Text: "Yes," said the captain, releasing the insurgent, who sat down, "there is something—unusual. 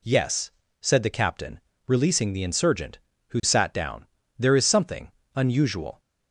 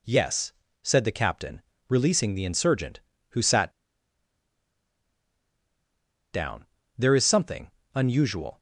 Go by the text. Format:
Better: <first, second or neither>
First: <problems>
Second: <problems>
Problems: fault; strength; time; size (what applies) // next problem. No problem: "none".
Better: first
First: none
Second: pauses between "sat" and "down"; strong; at 3.7 s; 2.6 s long